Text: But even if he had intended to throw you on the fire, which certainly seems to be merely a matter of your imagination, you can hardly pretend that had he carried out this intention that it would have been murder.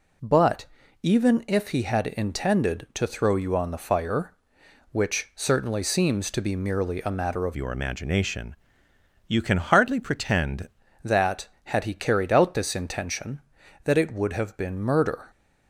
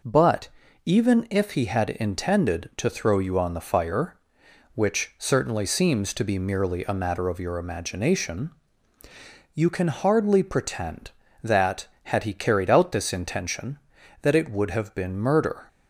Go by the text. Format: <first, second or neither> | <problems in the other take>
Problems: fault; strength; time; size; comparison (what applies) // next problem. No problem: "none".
second | pauses between "But" and "even"; slight; at 0.6 s; 0.36 s long; slight in the second // changes voice from "your" to "pretend"; from 7.5 to 10.6 s; 3.1 s long